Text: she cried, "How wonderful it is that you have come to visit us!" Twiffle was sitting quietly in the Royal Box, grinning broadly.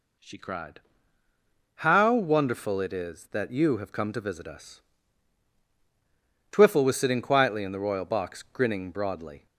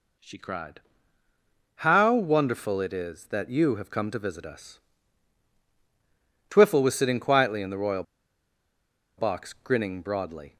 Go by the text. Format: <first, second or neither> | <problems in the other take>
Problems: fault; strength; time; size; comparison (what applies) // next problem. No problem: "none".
first | pauses between "Royal" and "Box"; at 8.0 s; 1.1 s long